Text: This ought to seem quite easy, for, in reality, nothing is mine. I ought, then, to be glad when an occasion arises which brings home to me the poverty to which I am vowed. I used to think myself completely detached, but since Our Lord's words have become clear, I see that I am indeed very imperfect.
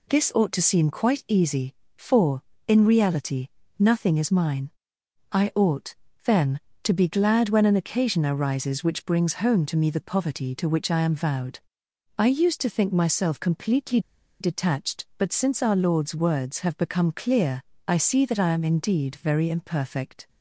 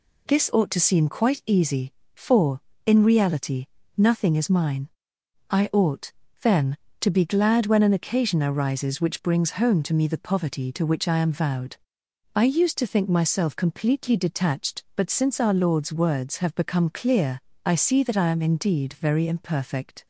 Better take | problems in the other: second | pauses between "completely" and "detached"; at 13.9 s; 0.41 s long

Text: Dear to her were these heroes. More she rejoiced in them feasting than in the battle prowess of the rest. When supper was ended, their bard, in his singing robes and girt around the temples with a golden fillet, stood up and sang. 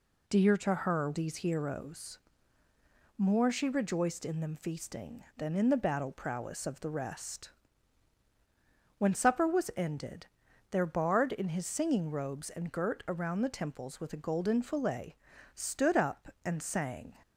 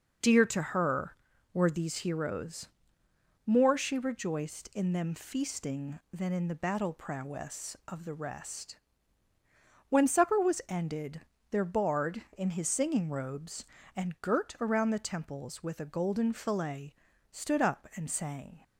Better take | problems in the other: second | skips "were"; at 1.1 s

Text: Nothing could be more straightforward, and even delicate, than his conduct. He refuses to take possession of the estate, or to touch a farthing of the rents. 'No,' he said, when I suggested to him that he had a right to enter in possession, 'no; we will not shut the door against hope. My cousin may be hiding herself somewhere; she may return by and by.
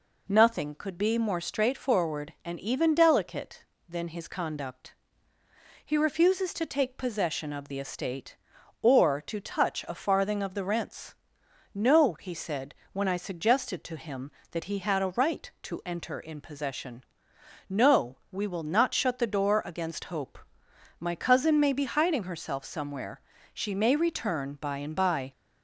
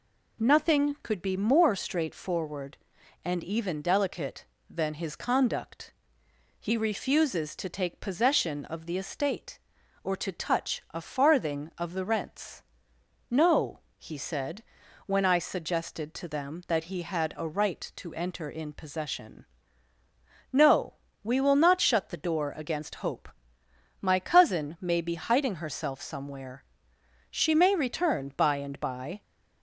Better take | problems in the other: first | says "them" for "him"; at 16.2 s

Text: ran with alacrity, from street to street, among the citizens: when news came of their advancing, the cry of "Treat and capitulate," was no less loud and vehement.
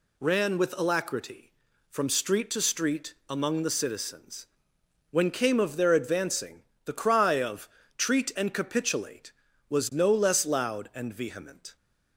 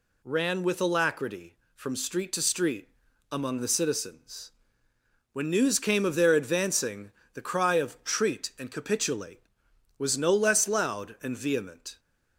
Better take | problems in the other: second | skips "news"; at 5.2 s // pauses between "of" and "Treat"; slight; at 7.6 s; 0.28 s long

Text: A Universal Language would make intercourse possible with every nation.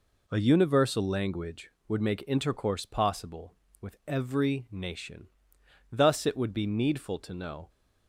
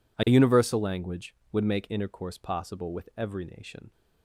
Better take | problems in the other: second | goes on to say "Thus it would be needful to know"; strong; from 5.9 s on; 1.7 s long

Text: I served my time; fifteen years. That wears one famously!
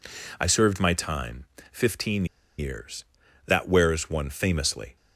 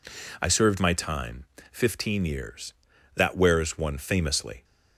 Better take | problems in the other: second | pauses between "fifteen" and "years"; slight; at 2.2 s; 0.33 s long

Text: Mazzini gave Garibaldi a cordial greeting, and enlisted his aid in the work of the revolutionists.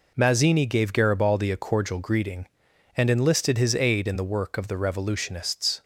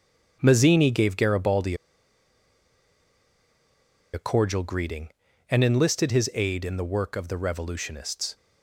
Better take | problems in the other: first | starts louder than the rest; strong; until 1.4 s; 7.5 dB // pauses between "Garibaldi" and "a"; strong; at 1.7 s; 2.3 s long

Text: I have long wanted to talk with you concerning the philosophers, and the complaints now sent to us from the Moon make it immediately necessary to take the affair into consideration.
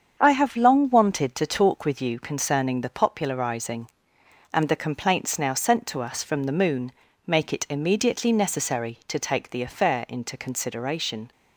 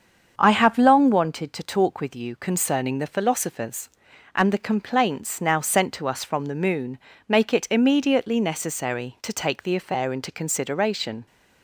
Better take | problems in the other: second | starts louder than the rest; strong; until 1.2 s; 7.5 dB; strong in the second // says "popularizing" for "philosophers"; at 2.8 s // pauses between "Moon" and "make"; slight; at 6.9 s; 0.34 s long; slight in the second

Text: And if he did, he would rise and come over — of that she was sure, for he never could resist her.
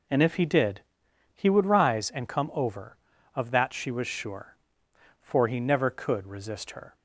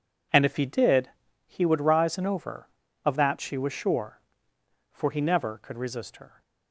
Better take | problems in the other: first | skips "come"; at 2.2 s

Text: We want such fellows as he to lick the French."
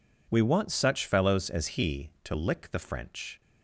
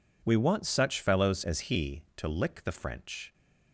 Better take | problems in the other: neither | none

